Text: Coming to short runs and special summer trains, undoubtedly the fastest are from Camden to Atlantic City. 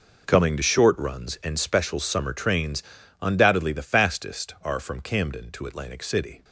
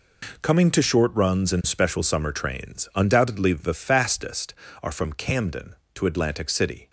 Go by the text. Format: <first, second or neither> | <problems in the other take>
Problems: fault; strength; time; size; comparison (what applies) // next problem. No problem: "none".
neither | none